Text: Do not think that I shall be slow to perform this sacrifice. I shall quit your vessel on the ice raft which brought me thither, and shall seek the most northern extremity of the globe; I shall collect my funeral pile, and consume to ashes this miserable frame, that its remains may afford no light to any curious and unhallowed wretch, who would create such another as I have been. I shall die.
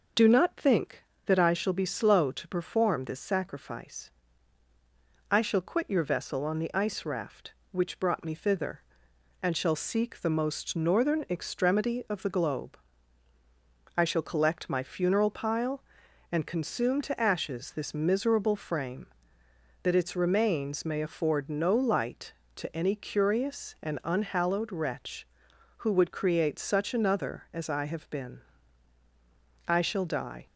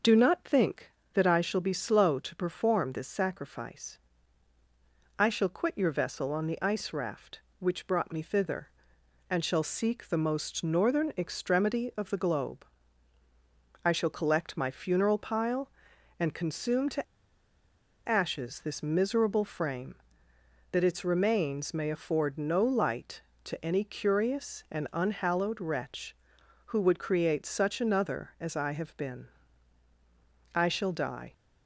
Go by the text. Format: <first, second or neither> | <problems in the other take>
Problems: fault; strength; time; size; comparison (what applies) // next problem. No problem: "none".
first | pauses between "to" and "ashes"; at 17.0 s; 1.0 s long